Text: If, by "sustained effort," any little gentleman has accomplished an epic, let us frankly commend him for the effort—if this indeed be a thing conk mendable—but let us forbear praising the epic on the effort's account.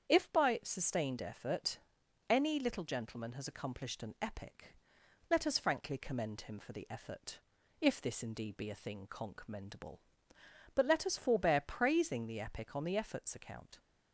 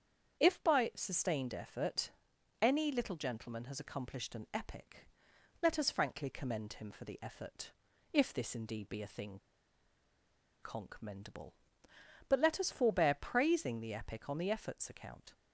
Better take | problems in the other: first | starts louder than the rest; strong; until 1.4 s; 8 dB; strong in the first // pauses between "thing" and "conk"; at 9.3 s; 1.2 s long

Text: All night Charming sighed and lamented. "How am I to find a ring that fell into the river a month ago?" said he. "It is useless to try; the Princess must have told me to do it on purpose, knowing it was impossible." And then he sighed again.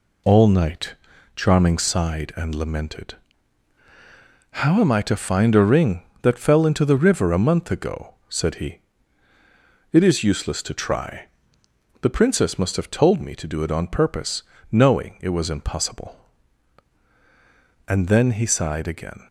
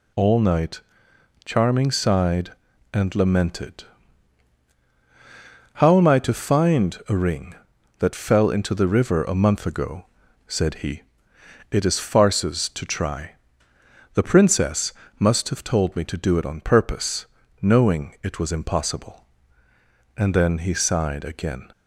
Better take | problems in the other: first | pauses between "night" and "Charming"; noticeable; at 0.8 s; 0.64 s long; also in the first // says "farces" for "useless"; at 11.9 s // pauses between "Princess" and "must"; slight; at 14.9 s; 0.26 s long

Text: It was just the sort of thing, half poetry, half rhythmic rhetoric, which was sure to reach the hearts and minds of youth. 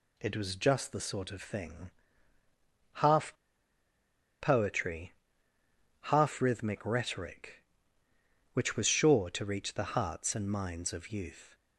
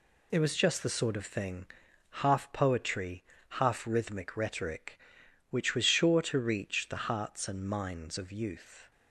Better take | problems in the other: second | pauses between "half" and "poetry"; at 3.3 s; 1.0 s long

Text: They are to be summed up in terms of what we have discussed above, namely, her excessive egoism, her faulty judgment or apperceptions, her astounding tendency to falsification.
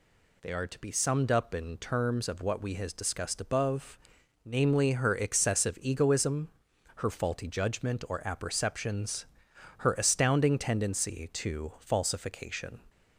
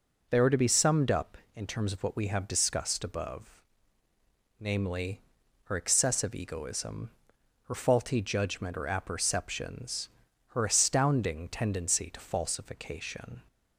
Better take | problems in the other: second | says "has" for "have"; at 2.7 s

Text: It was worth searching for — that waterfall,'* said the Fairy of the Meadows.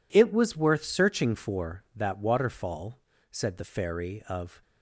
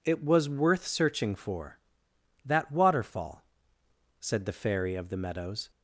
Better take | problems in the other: second | stops before "the Meadows"; at 4.6 s

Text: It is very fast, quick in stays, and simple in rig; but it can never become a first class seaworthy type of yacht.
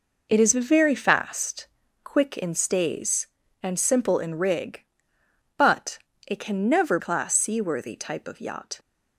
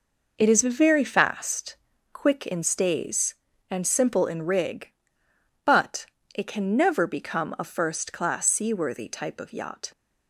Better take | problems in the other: second | pauses between "but" and "it"; slight; at 5.9 s; 0.28 s long; slight in the second // skips "become a first"; at 6.9 s

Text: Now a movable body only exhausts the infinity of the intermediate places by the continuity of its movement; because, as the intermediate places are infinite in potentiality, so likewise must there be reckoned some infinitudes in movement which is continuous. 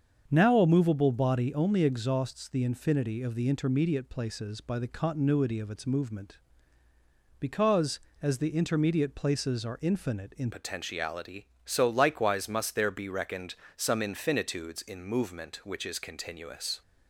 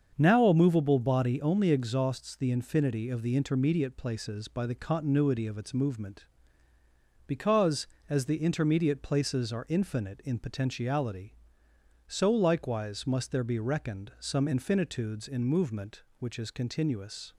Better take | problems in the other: second | starts louder than the rest; until 1.3 s; 7 dB; also in the second // changes voice at "potentiality"; from 10.5 s on; 6.3 s long // pauses between "reckoned" and "some"; slight; at 13.5 s; 0.22 s long

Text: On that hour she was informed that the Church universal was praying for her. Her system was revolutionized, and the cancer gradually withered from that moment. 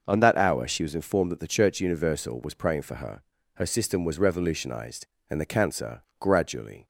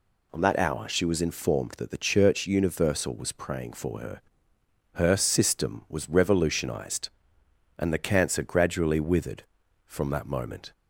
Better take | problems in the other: second | pauses between "cancer" and "gradually"; slight; at 6.0 s; 0.16 s long // stops before "withered from that moment"; at 6.8 s

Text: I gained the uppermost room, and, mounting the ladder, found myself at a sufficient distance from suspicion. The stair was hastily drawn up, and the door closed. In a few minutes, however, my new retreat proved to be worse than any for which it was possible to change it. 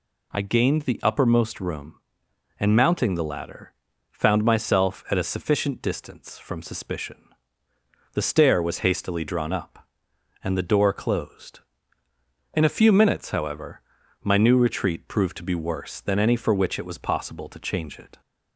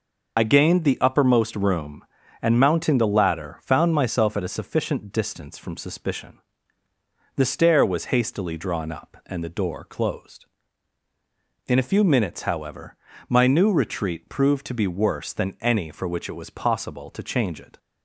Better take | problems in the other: first | loses the start of "I"; at 0.3 s; 40 ms

